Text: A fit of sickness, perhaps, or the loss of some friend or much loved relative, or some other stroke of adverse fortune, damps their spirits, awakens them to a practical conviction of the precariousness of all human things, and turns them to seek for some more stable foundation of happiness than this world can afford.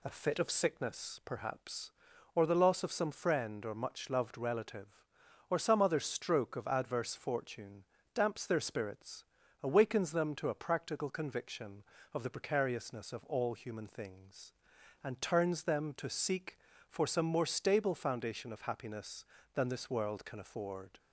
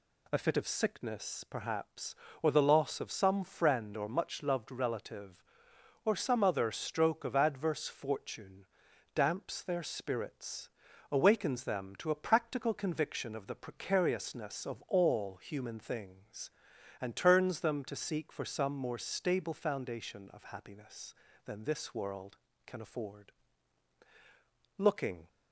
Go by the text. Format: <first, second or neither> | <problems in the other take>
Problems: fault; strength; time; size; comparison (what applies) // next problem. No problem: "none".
first | goes on to say "Looking"; from 24.7 s on; 0.50 s long